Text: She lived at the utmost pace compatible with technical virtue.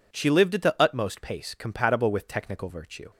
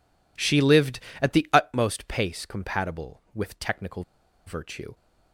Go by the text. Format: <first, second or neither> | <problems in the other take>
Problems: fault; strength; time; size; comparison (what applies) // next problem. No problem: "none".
first | pauses between "technical" and "virtue"; at 4.0 s; 0.44 s long